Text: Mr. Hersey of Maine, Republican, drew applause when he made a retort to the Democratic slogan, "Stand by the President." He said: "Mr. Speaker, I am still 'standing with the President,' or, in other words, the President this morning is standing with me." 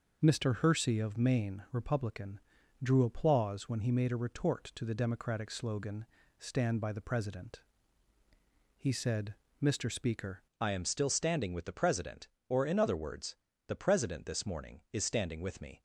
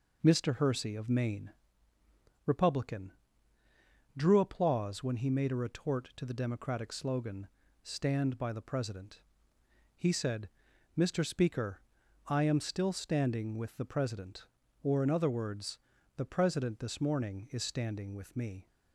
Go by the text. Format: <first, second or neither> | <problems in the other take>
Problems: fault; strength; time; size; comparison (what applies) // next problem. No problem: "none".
second | changes voice at "I"; from 10.6 s on; 5.2 s long